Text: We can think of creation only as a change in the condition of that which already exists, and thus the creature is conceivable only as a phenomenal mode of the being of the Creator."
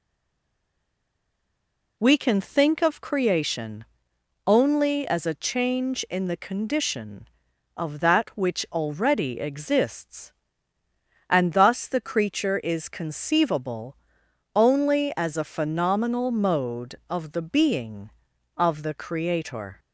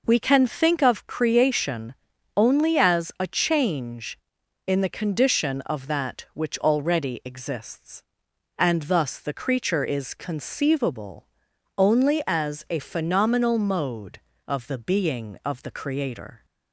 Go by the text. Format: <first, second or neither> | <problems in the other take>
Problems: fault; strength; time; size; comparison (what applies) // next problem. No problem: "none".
second | stays silent before the first word; noticeable; until 1.9 s; 1.9 s long // pauses between "creation" and "only"; noticeable; at 3.8 s; 0.60 s long; also in the second // pauses between "conceivable" and "only"; noticeable; at 13.9 s; 0.60 s long; noticeable in the second